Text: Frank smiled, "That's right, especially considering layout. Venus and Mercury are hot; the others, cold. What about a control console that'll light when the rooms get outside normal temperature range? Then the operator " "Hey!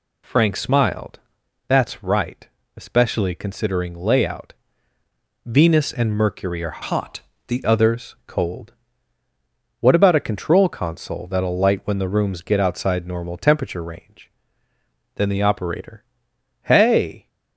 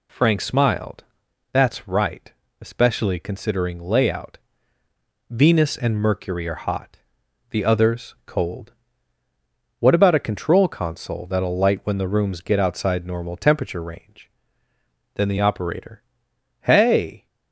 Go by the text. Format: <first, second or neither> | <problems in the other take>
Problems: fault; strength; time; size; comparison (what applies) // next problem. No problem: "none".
second | changes voice from "hot" to "the"; from 6.8 to 7.6 s; 0.8 s long